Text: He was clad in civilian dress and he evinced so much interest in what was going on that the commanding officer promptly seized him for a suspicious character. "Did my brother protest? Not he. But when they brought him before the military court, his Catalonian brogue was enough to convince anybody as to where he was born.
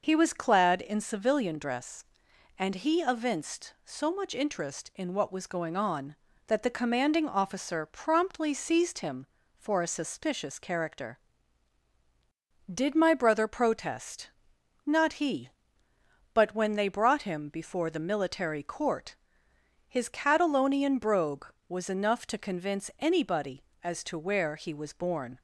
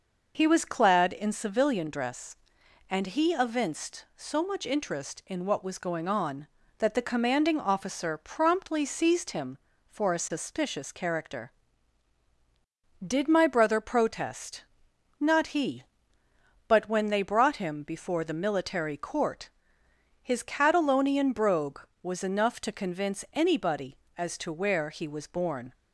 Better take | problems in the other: neither | none

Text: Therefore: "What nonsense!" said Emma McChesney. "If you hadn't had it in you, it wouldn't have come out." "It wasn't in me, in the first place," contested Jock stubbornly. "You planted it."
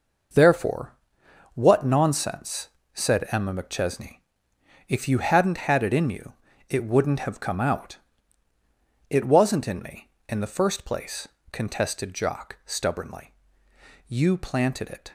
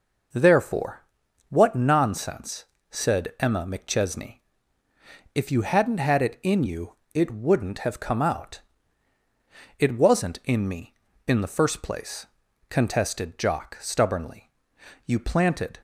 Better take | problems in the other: first | stops before "it"; at 15.7 s

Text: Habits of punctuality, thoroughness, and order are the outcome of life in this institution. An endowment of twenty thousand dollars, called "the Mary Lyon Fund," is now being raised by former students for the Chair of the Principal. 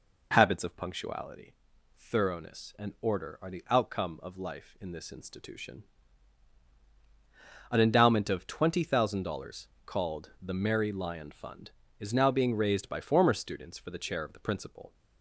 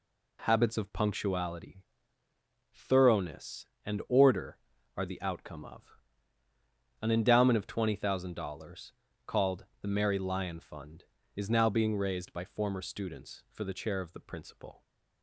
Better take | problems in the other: first | skips "life in this institution"; at 6.4 s // pauses between "called" and "the"; slight; at 9.6 s; 0.16 s long

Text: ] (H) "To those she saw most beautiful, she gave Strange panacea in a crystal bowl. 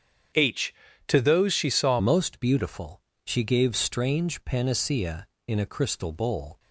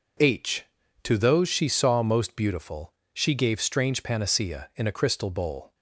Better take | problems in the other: second | starts louder than the rest; strong; until 1.6 s; 8 dB // changes voice at "most"; from 1.9 s on; 4.6 s long

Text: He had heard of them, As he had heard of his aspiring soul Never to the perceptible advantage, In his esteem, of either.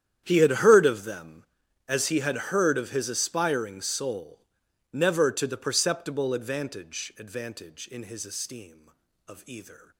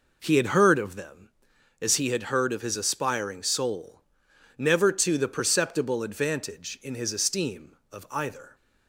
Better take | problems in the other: second | starts louder than the rest; strong; until 1.2 s; 10 dB // pauses between "soul" and "Never"; noticeable; at 4.3 s; 0.54 s long; noticeable in the second // says "advantage" twice; at 7.1 s

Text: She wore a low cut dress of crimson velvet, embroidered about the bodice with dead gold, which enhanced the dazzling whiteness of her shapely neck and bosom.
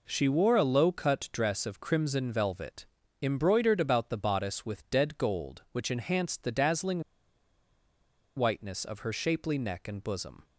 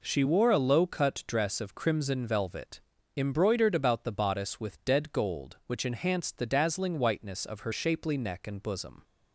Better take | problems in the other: second | pauses between "dazzling" and "whiteness"; strong; at 7.0 s; 1.3 s long

